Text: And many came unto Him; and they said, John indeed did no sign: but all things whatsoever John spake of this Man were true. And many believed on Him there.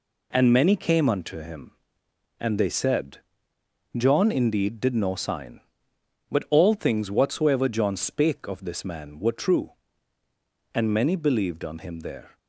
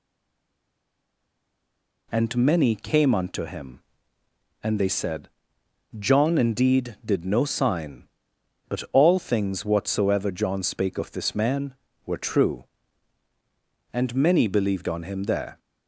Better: first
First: none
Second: stays silent before the first word; until 2.1 s; 2.1 s long

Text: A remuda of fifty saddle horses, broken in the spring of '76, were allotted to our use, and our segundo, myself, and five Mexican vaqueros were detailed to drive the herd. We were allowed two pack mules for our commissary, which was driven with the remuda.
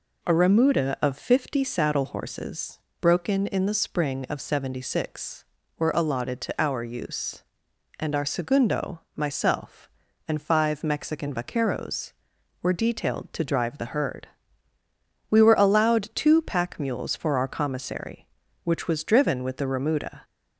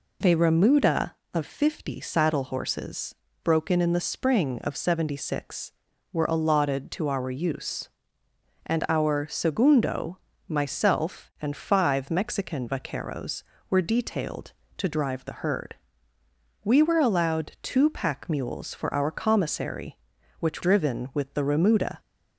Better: first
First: none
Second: skips "was"; at 20.6 s

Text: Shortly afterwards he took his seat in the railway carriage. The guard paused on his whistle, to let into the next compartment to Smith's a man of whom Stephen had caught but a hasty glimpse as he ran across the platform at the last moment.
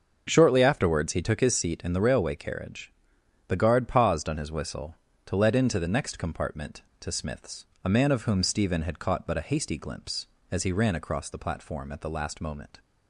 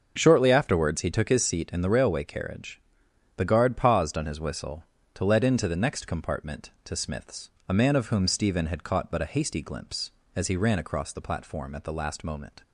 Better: neither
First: starts louder than the rest; until 1.2 s; 6 dB // pauses between "Smith's" and "a"; slight; at 7.6 s; 0.18 s long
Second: starts louder than the rest; until 1.1 s; 6 dB // pauses between "Smith's" and "a"; slight; at 7.5 s; 0.18 s long

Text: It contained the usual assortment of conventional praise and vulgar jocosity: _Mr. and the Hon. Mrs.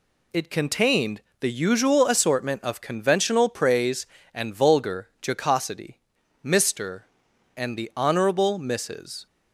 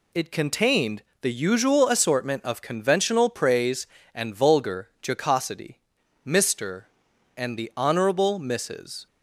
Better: neither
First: pauses between "contained" and "the"; slight; at 1.2 s; 0.20 s long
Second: pauses between "contained" and "the"; slight; at 1.0 s; 0.20 s long

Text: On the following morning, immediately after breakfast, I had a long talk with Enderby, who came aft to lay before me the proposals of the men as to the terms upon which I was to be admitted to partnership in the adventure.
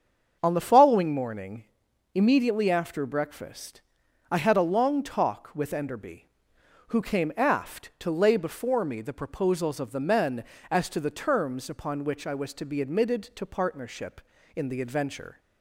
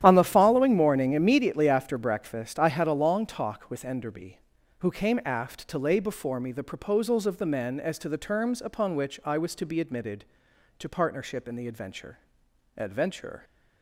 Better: first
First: starts louder than the rest; until 1.4 s; 7 dB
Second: starts louder than the rest; strong; until 1.0 s; 11 dB // says "adventure" twice; at 12.7 s

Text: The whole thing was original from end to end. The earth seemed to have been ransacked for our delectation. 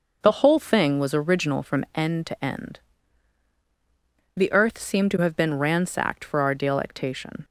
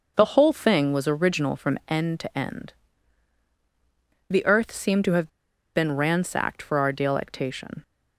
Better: first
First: none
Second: pauses between "have" and "been"; noticeable; at 5.2 s; 0.48 s long

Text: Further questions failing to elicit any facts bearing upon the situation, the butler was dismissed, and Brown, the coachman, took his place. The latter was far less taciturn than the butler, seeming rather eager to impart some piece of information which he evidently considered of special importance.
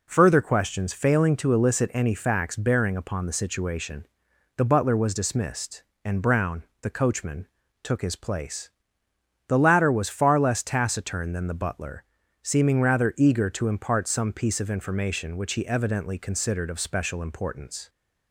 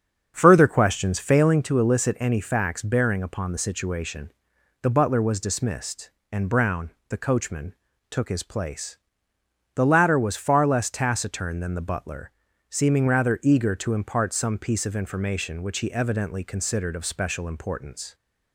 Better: first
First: none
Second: starts louder than the rest; strong; until 1.6 s; 7.5 dB

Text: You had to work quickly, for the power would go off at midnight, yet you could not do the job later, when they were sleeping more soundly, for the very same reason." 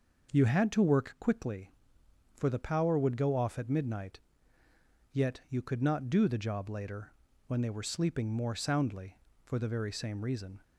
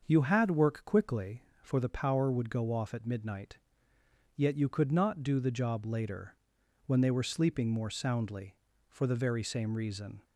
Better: first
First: none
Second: starts louder than the rest; until 1.0 s; 6.5 dB // skips "to"; at 0.4 s

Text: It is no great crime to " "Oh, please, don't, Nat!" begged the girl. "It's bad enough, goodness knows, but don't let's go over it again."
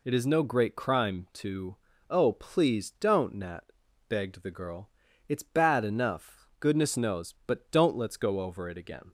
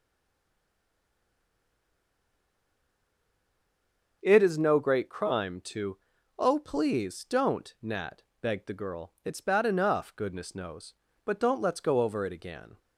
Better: first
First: none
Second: stays silent before the first word; strong; until 4.2 s; 4.2 s long // starts louder than the rest; noticeable; until 5.2 s; 6 dB

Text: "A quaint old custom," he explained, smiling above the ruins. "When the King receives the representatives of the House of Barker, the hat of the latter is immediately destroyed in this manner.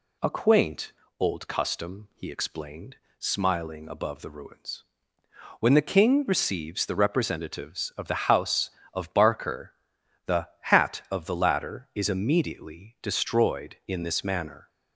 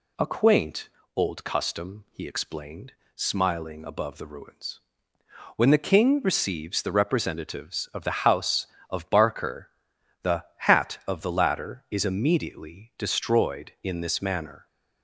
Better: neither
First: pauses between "quaint" and "old"; slight; at 0.9 s; 0.30 s long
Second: pauses between "quaint" and "old"; slight; at 0.8 s; 0.30 s long

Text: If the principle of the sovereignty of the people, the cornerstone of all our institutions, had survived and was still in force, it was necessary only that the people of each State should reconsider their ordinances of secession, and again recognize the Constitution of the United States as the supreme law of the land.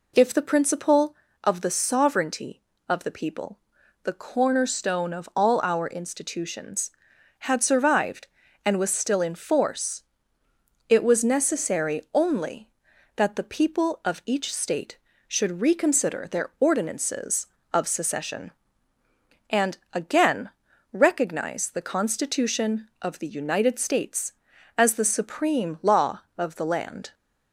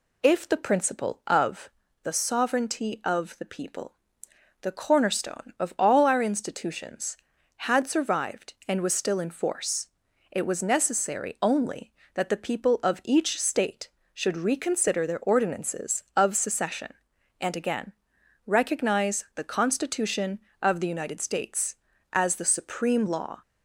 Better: first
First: pauses between "again" and "recognize"; at 20.5 s; 0.42 s long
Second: pauses between "of" and "the"; slight; at 1.7 s; 0.32 s long // pauses between "again" and "recognize"; noticeable; at 17.9 s; 0.52 s long // stops before "of the land"; at 23.4 s

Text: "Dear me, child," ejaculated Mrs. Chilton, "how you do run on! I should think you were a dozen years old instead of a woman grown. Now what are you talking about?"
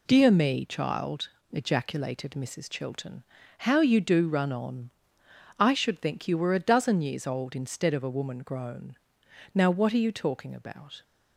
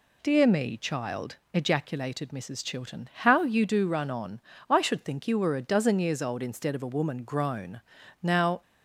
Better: first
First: none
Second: stops before "what are you talking about"; at 8.6 s

